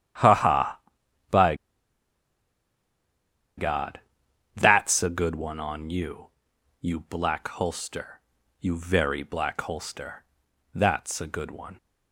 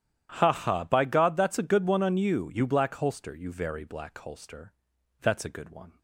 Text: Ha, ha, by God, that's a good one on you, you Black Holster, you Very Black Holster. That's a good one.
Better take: second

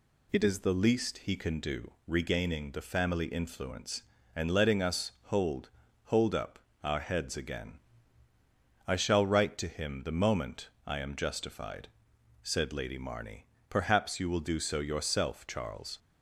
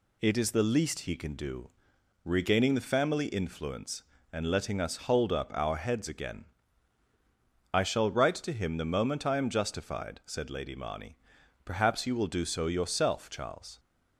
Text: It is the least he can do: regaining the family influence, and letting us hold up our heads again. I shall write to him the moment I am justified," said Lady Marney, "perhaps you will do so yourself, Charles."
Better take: second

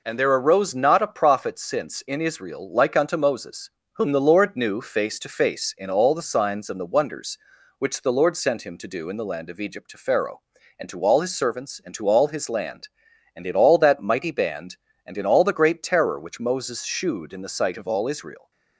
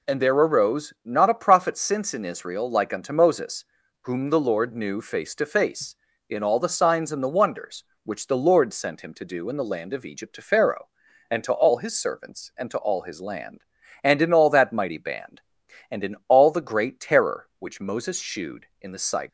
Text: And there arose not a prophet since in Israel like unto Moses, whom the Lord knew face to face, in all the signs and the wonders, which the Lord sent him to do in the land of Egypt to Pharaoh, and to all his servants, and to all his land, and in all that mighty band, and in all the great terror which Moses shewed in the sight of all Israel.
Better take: first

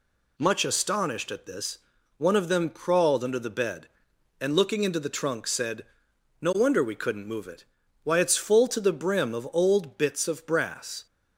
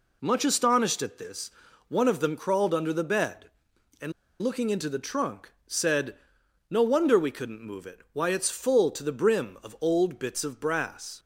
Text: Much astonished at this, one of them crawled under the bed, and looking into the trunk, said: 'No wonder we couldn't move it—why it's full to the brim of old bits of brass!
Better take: first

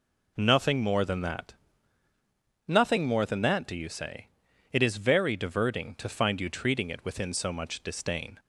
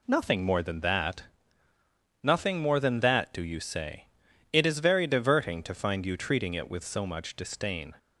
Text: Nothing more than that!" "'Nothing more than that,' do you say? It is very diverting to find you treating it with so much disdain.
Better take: second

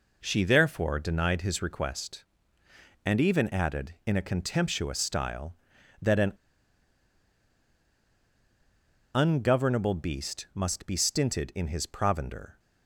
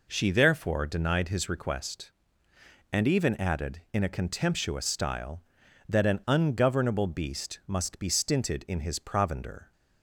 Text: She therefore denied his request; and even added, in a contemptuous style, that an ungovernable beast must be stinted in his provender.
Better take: second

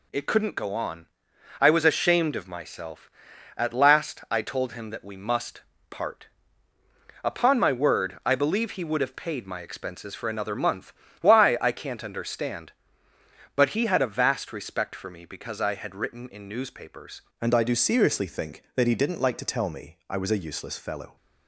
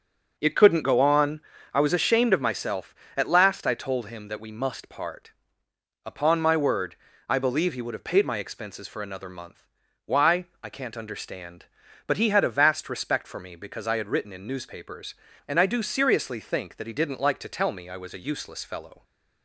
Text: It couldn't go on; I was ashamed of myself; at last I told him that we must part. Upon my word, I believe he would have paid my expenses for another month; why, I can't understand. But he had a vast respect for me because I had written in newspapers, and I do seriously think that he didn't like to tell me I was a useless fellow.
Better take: second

